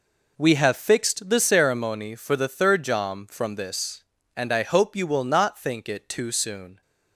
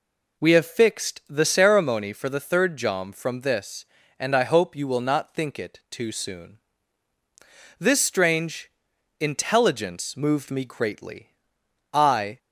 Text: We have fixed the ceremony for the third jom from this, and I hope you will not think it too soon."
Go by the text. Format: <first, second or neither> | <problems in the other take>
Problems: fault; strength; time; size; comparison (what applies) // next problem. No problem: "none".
first | goes on to say "This strange intelligence moved me greatly I"; strong; from 7.7 s on; 4.5 s long